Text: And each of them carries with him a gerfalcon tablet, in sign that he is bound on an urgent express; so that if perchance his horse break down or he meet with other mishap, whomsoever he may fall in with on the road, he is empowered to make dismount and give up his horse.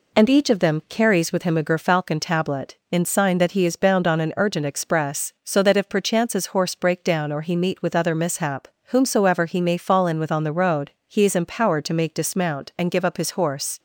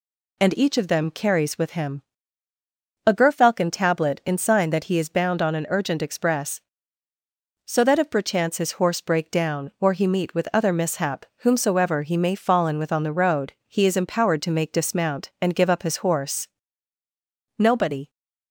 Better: first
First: none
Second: pauses between "him" and "a"; at 2.0 s; 1.0 s long // goes on to say "Nobody"; from 17.5 s on; 0.50 s long

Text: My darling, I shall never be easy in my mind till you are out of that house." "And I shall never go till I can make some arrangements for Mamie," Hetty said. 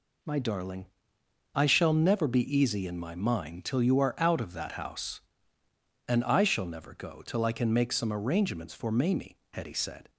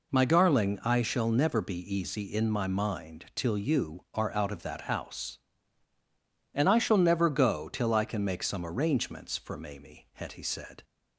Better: neither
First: none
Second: none

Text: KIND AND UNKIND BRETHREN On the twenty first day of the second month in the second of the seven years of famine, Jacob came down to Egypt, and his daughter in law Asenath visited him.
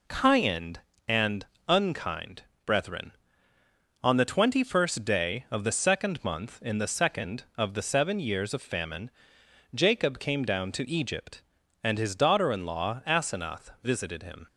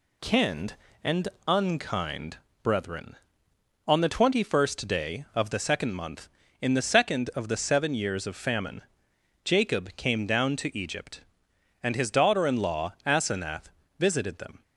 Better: first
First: pauses between "AND" and "UNKIND"; slight; at 1.4 s; 0.22 s long // pauses between "UNKIND" and "BRETHREN"; slight; at 2.4 s; 0.20 s long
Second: pauses between "AND" and "UNKIND"; slight; at 1.2 s; 0.18 s long // pauses between "UNKIND" and "BRETHREN"; slight; at 2.3 s; 0.24 s long // pauses between "Asenath" and "visited"; slight; at 13.6 s; 0.28 s long // says "them" for "him"; at 14.3 s

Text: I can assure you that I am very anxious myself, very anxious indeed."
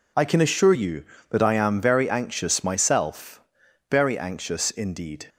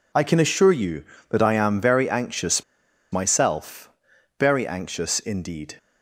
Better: first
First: none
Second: pauses between "anxious" and "myself"; noticeable; at 2.6 s; 0.48 s long

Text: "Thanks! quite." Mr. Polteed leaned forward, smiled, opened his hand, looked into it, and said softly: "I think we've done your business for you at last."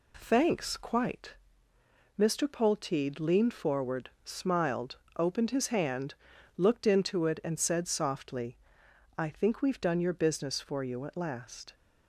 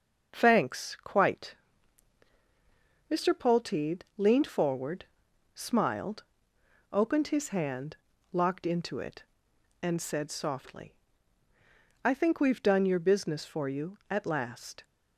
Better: first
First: none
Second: starts louder than the rest; until 1.3 s; 6 dB // says "locked" for "looked"; at 8.3 s

